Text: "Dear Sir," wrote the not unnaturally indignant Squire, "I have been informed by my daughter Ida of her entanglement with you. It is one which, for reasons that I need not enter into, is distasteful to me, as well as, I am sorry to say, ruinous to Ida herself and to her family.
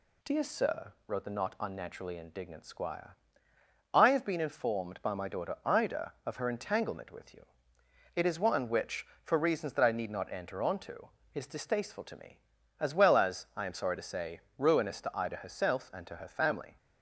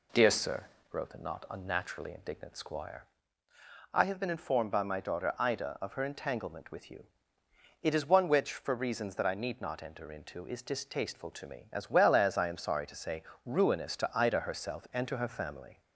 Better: second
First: says "onto" for "into"; at 10.6 s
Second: none

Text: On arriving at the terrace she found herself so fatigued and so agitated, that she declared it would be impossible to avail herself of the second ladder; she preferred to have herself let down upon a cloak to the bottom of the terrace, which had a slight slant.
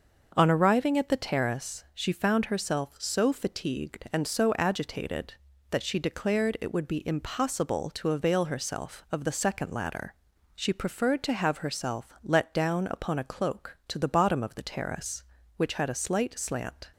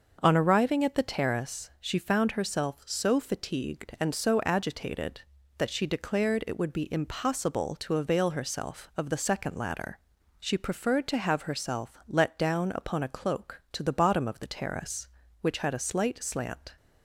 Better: neither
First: starts louder than the rest; until 1.3 s; 6.5 dB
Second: starts louder than the rest; until 1.2 s; 6.5 dB

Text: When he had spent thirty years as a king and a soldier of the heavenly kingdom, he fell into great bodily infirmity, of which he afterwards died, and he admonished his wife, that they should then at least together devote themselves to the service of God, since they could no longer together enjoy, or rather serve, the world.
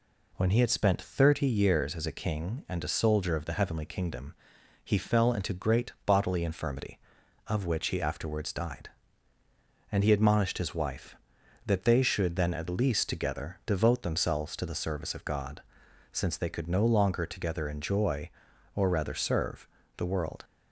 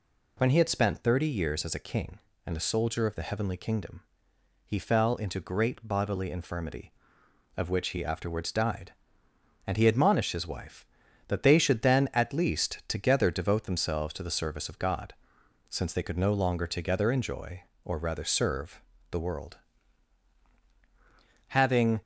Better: first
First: none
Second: goes on to say "Having"; from 21.4 s on; 0.52 s long

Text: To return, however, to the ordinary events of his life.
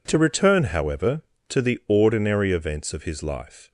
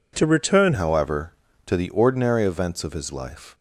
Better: first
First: none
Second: changes voice at "however"; from 0.7 s on; 2.8 s long

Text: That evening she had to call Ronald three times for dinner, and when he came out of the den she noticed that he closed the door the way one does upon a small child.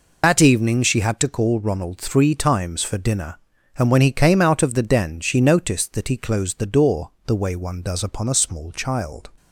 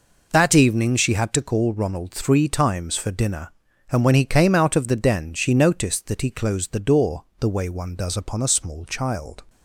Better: second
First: loses the start of "That"; at 0.2 s; 65 ms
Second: none

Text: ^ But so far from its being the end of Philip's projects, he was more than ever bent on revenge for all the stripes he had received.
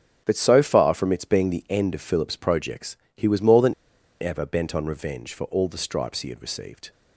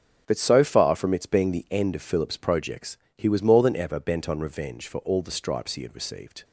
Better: second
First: starts louder than the rest; until 1.2 s; 7 dB // pauses between "than" and "ever"; noticeable; at 3.7 s; 0.48 s long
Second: starts louder than the rest; strong; until 1.2 s; 7 dB

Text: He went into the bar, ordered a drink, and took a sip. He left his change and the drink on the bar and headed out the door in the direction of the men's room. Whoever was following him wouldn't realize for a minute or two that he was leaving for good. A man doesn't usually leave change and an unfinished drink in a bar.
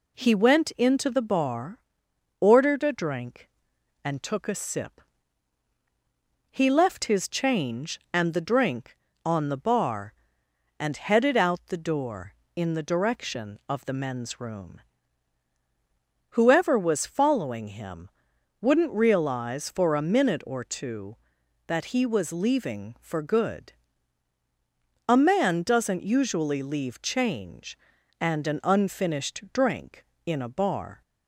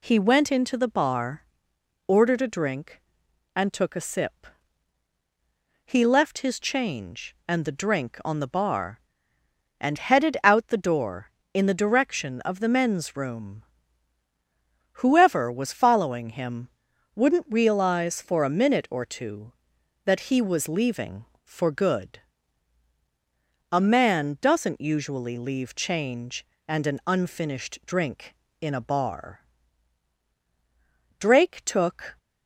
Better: first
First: pauses between "him" and "wouldn't"; noticeable; at 18.0 s; 0.52 s long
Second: pauses between "him" and "wouldn't"; noticeable; at 16.6 s; 0.48 s long // goes on to say "Drake took"; noticeable; from 31.1 s on; 0.98 s long

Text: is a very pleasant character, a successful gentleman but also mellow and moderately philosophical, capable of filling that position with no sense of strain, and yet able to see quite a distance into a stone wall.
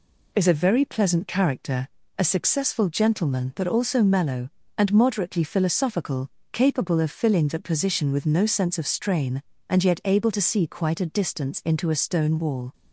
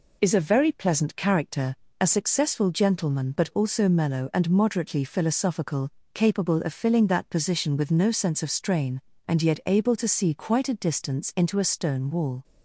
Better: neither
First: none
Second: none

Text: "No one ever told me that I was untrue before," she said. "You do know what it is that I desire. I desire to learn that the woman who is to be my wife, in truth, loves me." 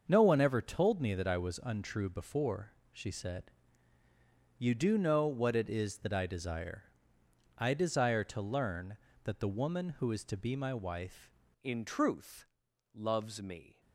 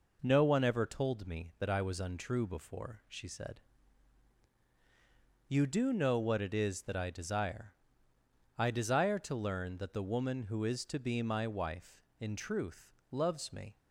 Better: second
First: starts louder than the rest; until 1.0 s; 6.5 dB // changes voice at "in"; from 11.6 s on; 2.2 s long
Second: none

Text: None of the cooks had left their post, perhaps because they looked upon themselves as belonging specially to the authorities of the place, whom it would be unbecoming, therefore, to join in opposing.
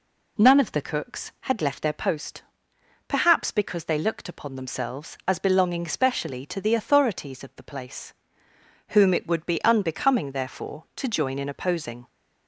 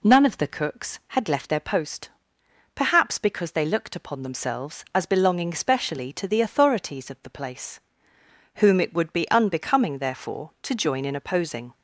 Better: neither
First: none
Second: none

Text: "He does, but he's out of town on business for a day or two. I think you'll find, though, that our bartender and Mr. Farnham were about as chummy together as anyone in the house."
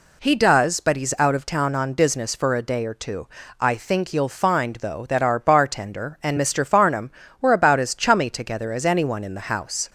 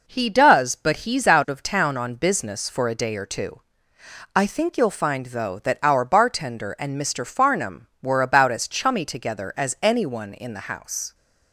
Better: neither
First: none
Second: none

